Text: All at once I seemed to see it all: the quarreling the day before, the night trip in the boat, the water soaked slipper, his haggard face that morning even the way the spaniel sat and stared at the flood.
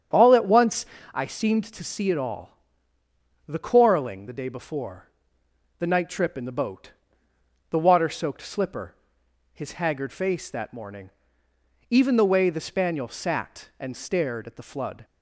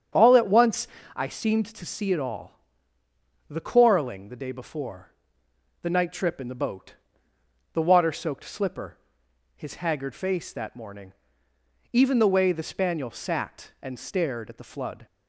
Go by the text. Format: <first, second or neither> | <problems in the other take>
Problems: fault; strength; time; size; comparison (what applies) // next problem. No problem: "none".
neither | starts louder than the rest; strong; the same in both // pauses between "once" and "I"; slight; the same in both // pauses between "morning" and "even"; noticeable; the same in both